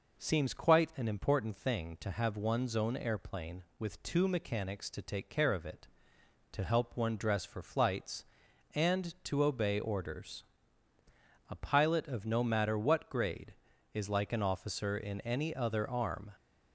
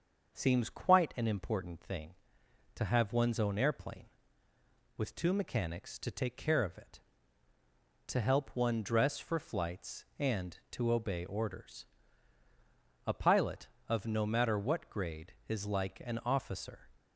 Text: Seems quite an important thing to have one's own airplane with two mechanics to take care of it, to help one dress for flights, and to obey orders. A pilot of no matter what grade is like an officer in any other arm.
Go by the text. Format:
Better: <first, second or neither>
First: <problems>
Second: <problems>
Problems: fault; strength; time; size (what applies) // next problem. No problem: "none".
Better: first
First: none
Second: starts louder than the rest; until 1.3 s; 6 dB // stops before "in any other arm"; at 16.9 s